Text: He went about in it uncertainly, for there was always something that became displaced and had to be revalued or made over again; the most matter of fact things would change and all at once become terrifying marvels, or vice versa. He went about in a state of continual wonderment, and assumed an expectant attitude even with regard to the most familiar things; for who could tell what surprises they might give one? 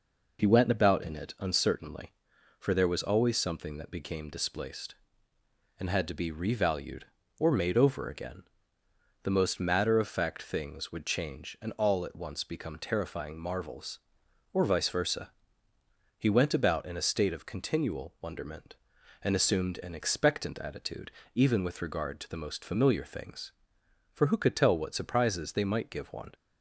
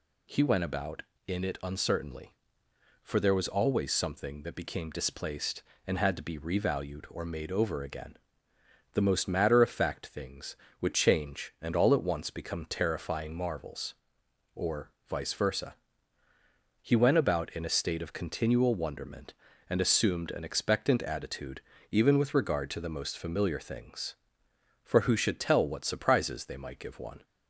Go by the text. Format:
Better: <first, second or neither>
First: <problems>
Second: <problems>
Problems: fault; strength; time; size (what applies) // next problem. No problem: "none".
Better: first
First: pauses between "attitude" and "even"; slight; at 21.1 s; 0.24 s long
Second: pauses between "or" and "vice"; slight; at 14.9 s; 0.16 s long // pauses between "attitude" and "even"; slight; at 21.6 s; 0.28 s long // says "should" for "could"; at 25.1 s